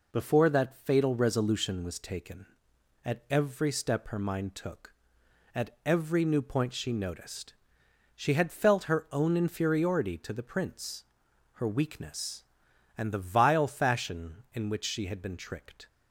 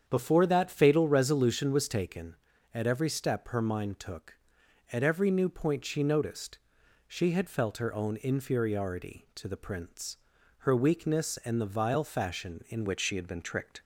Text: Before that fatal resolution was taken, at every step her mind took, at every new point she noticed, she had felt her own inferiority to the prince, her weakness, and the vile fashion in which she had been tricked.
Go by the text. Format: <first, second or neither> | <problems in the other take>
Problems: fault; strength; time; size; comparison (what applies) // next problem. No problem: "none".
first | starts louder than the rest; strong; until 1.0 s; 8 dB // changes voice at "which"; from 12.8 s on; 1.0 s long